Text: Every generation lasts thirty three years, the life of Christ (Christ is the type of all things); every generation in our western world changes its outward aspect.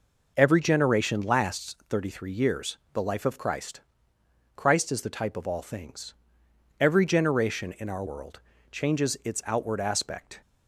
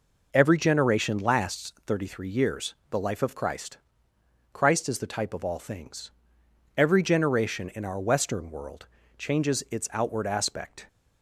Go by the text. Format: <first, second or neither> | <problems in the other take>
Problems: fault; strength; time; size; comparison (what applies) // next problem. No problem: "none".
second | skips "western"; at 8.0 s // pauses between "world" and "changes"; slight; at 8.4 s; 0.32 s long; slight in the second